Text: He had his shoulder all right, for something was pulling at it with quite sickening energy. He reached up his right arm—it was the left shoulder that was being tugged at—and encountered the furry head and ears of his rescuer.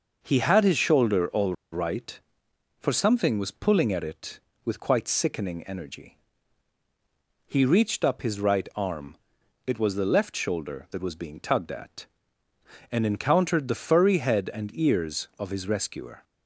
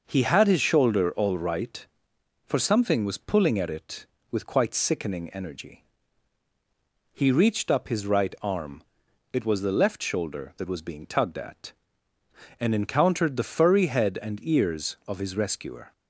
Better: second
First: pauses between "all" and "right"; slight; at 1.5 s; 0.18 s long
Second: none

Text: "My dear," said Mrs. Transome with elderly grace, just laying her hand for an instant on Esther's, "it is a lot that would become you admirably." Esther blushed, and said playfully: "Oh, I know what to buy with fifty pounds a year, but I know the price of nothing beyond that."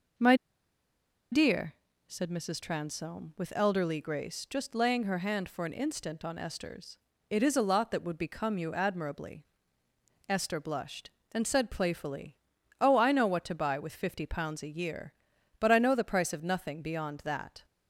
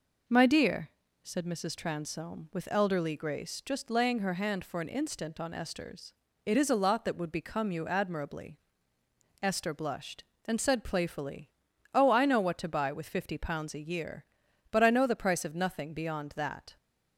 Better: second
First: pauses between "My" and "dear"; noticeable; at 0.3 s; 0.97 s long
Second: none

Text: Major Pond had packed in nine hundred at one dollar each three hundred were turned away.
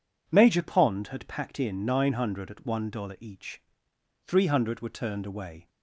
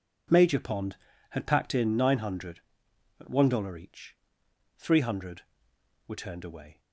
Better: neither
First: pauses between "each" and "three"; noticeable; at 3.6 s; 0.66 s long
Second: pauses between "each" and "three"; noticeable; at 4.1 s; 0.62 s long

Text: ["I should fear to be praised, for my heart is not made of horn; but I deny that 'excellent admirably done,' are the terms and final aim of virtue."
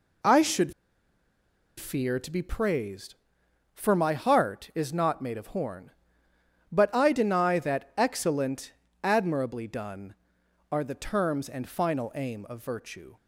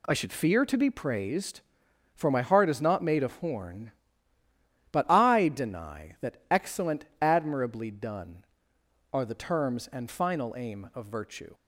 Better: second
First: pauses between "should" and "fear"; at 0.7 s; 1.0 s long // pauses between "excellent" and "admirably"; slight; at 8.7 s; 0.28 s long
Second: pauses between "excellent" and "admirably"; slight; at 7.0 s; 0.16 s long

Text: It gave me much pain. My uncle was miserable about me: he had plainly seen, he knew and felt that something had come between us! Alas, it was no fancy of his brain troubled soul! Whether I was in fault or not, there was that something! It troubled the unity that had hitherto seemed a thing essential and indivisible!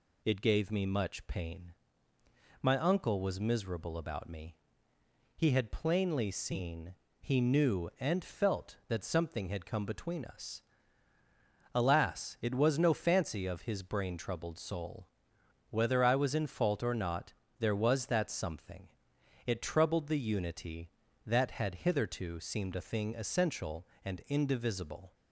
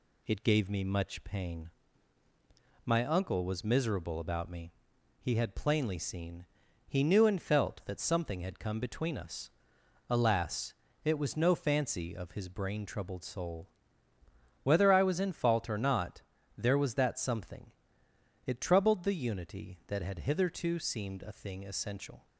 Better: first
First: none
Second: stops before "and indivisible"; at 22.2 s

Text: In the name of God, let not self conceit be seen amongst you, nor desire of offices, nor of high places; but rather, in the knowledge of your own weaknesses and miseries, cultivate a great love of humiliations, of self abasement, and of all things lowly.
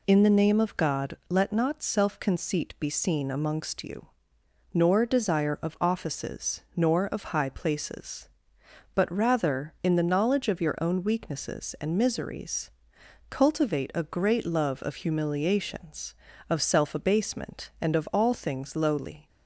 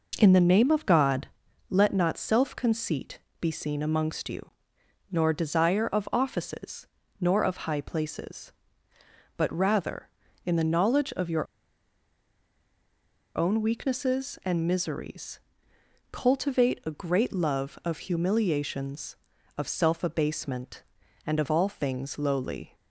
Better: first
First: none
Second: pauses between "conceit" and "be"; slight; at 3.1 s; 0.22 s long // pauses between "your" and "own"; strong; at 11.4 s; 1.9 s long

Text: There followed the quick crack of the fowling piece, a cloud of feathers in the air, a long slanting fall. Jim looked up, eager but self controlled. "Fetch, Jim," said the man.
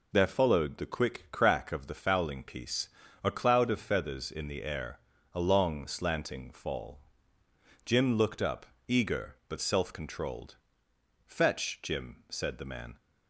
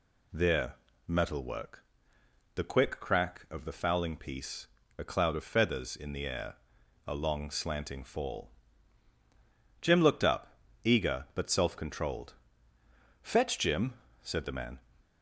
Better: first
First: none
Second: says "metalwork" for "followed"; at 1.0 s

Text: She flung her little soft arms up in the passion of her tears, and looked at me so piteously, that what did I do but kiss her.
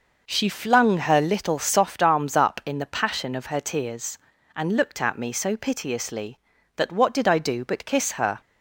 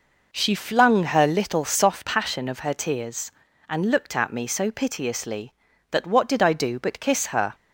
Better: first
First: none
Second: skips "arms up in the"; at 2.0 s

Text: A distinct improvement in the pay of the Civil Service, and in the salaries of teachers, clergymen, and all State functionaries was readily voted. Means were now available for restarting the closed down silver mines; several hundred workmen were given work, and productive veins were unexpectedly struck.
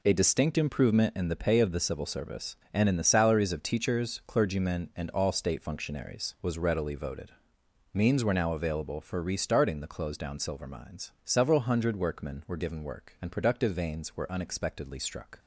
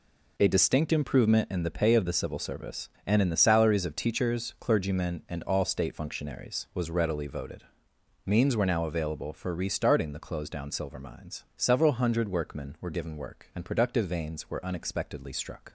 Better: neither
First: none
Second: none

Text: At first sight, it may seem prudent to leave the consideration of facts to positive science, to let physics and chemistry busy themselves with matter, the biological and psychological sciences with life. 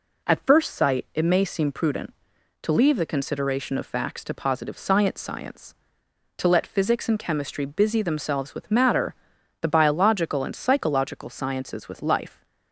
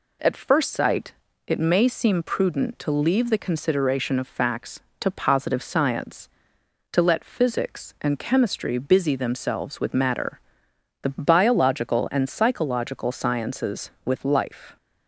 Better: second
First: says "science" twice; at 5.2 s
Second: none

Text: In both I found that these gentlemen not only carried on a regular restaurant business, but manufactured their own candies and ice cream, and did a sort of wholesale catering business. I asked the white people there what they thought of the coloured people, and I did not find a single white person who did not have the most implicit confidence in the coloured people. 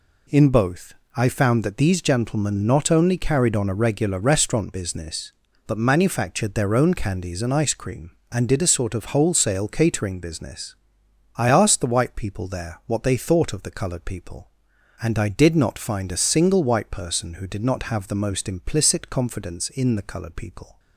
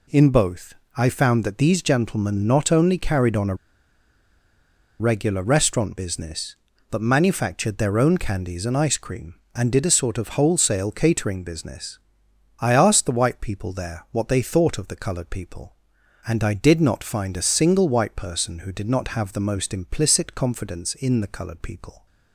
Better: first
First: pauses between "both" and "I"; slight; at 0.9 s; 0.22 s long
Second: pauses between "both" and "I"; slight; at 0.7 s; 0.22 s long // pauses between "a" and "regular"; strong; at 3.5 s; 1.4 s long

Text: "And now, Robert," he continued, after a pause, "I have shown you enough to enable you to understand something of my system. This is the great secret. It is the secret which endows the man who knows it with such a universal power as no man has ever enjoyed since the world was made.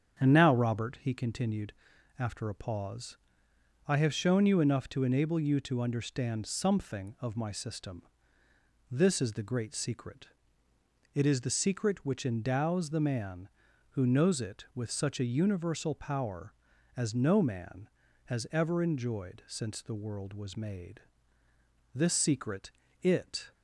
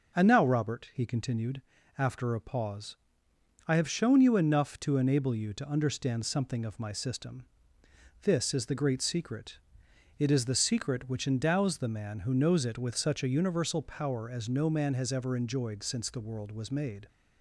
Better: second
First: starts louder than the rest; strong; until 1.2 s; 8 dB // goes on to say "This secret it"; from 21.9 s on; 1.5 s long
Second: none

